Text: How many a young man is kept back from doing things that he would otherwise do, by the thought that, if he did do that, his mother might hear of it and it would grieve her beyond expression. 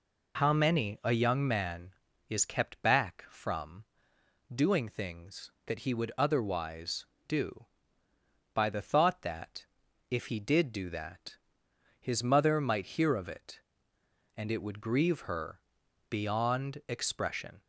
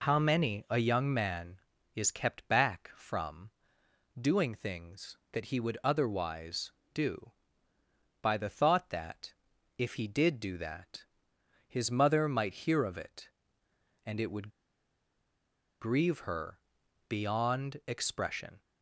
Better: first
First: pauses between "from" and "doing"; noticeable; at 3.8 s; 0.68 s long // pauses between "her" and "beyond"; noticeable; at 15.5 s; 0.50 s long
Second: pauses between "from" and "doing"; noticeable; at 3.5 s; 0.68 s long // pauses between "would" and "grieve"; strong; at 14.5 s; 1.3 s long // pauses between "her" and "beyond"; noticeable; at 16.5 s; 0.50 s long

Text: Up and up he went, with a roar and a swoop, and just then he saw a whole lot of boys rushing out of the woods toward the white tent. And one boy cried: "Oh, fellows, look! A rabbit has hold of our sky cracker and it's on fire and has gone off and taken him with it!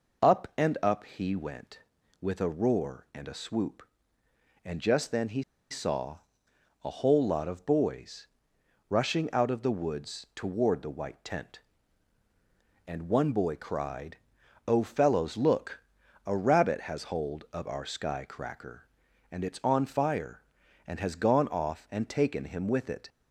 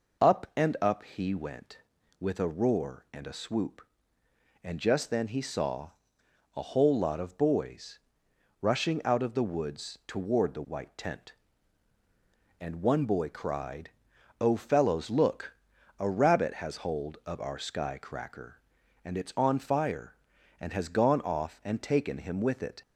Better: second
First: pauses between "he" and "saw"; slight; at 5.4 s; 0.27 s long // pauses between "saw" and "a"; noticeable; at 6.1 s; 0.64 s long // pauses between "boys" and "rushing"; noticeable; at 8.2 s; 0.64 s long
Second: pauses between "saw" and "a"; noticeable; at 5.9 s; 0.64 s long // pauses between "boys" and "rushing"; noticeable; at 7.9 s; 0.64 s long

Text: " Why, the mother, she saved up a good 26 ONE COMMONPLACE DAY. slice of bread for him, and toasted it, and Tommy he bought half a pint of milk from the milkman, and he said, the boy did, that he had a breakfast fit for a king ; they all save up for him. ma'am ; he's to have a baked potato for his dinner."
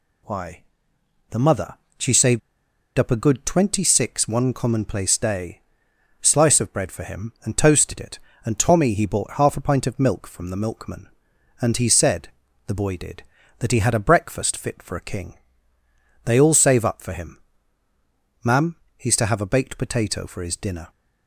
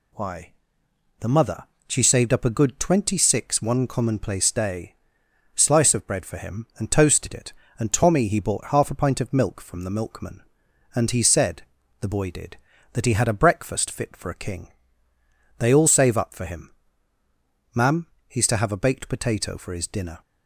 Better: second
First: pauses between "saved" and "up"; noticeable; at 2.4 s; 0.57 s long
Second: none

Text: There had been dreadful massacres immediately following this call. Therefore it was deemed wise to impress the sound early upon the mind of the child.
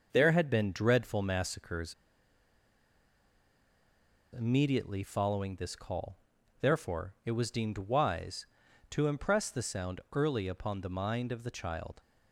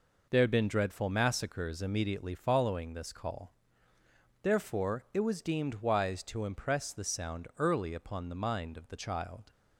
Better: second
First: starts louder than the rest; until 1.1 s; 6 dB // pauses between "massacres" and "immediately"; strong; at 1.9 s; 2.4 s long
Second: none

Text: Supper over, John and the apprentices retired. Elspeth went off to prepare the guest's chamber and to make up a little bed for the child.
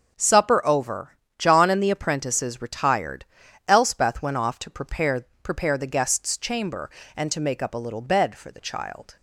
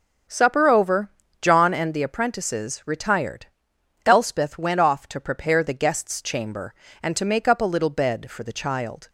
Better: second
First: starts louder than the rest; until 1.1 s; 6.5 dB // says "prepare" twice; at 5.4 s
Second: starts louder than the rest; until 1.6 s; 7 dB

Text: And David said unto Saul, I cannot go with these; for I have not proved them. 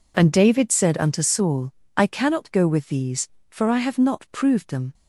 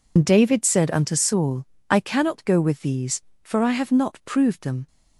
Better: first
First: none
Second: loses the start of "And"; at 0.1 s; 80 ms

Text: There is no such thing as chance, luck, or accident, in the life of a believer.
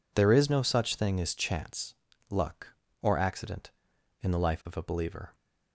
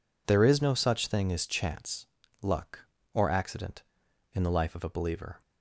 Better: neither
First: none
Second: none

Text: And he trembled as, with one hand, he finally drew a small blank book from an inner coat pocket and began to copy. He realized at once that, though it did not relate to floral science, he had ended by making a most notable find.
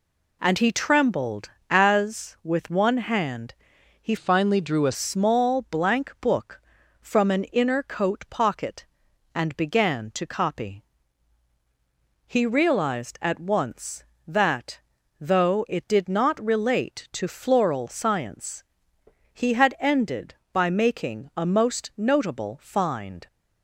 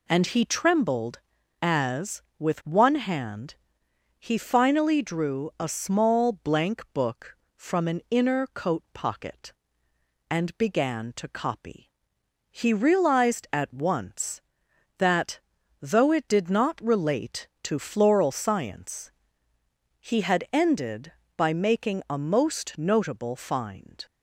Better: second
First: changes voice from "finally" to "a"; from 4.1 to 4.9 s; 0.8 s long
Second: none

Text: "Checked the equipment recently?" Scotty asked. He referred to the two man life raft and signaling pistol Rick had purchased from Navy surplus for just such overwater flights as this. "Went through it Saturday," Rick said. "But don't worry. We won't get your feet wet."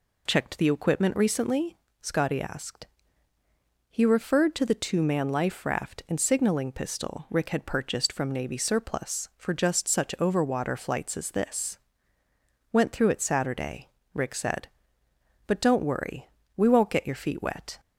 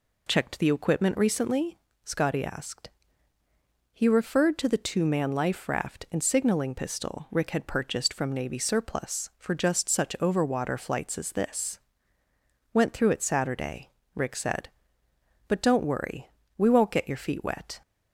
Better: neither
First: none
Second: none

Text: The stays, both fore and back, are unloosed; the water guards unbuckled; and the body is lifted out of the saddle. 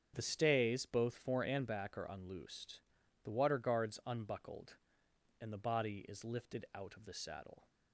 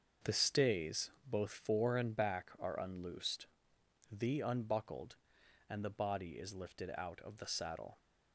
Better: first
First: starts louder than the rest; strong; until 1.1 s; 7.5 dB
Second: starts louder than the rest; until 1.3 s; 6 dB // skips "water guards"; at 4.4 s

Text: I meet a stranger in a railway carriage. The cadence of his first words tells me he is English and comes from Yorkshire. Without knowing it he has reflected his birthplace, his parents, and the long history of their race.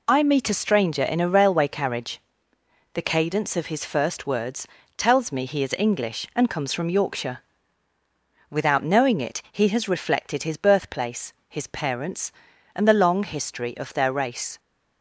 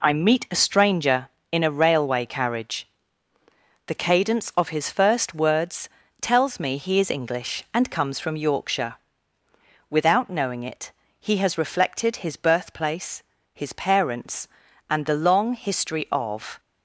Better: first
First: pauses between "words" and "tells"; slight; at 4.6 s; 0.30 s long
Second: pauses between "words" and "tells"; slight; at 5.8 s; 0.32 s long // pauses between "it" and "he"; slight; at 10.8 s; 0.30 s long // stops before "their race"; at 16.5 s

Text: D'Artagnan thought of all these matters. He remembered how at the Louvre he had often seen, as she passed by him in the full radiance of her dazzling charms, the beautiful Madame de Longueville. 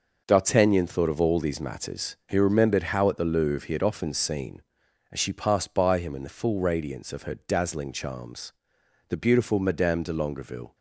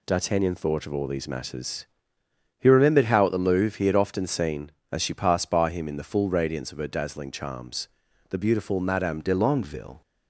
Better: first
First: none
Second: changes voice at "de"; from 9.1 s on; 0.9 s long

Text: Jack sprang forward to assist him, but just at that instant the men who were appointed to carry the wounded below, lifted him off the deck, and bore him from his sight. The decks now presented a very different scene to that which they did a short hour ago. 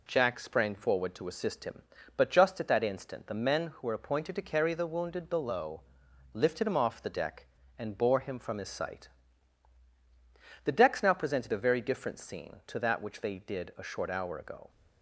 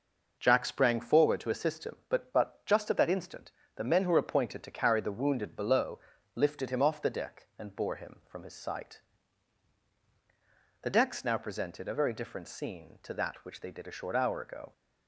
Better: first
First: none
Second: says "but" twice; at 2.3 s // pauses between "instant" and "the"; slight; at 3.5 s; 0.26 s long

